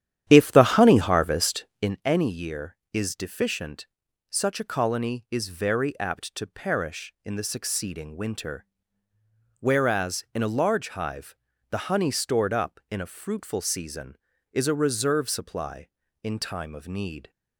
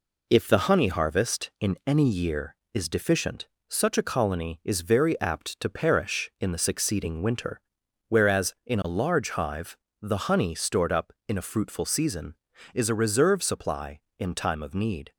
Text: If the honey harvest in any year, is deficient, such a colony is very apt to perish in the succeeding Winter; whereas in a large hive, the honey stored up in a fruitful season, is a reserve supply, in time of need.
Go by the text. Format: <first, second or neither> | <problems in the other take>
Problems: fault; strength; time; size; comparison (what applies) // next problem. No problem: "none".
second | starts louder than the rest; strong; until 2.0 s; 11 dB